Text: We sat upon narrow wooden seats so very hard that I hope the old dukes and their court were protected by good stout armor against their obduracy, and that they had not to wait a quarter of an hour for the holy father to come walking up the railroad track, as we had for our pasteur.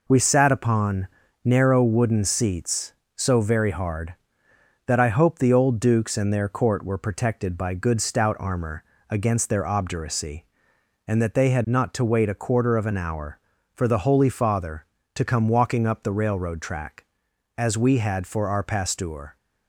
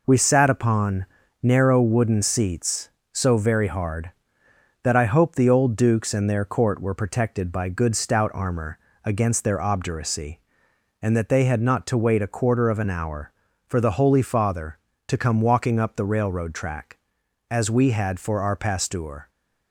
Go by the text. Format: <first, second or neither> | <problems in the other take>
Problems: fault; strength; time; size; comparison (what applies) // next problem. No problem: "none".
neither | pauses between "upon" and "narrow"; slight; the same in both // pauses between "armor" and "against"; slight; the same in both